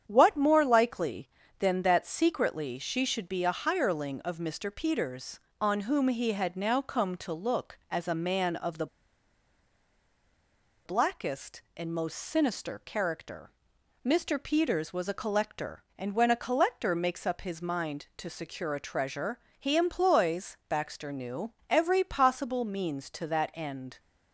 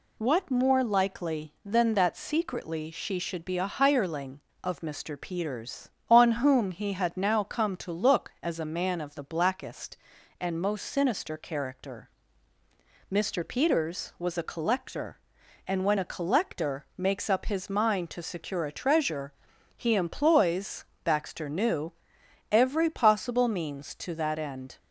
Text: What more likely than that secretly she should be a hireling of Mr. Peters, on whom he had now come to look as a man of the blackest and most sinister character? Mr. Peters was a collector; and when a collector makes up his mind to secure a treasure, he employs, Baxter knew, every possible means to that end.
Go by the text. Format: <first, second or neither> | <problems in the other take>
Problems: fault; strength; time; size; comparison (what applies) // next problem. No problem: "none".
second | starts louder than the rest; strong; until 1.0 s; 8.5 dB // pauses between "the" and "blackest"; strong; at 8.8 s; 1.9 s long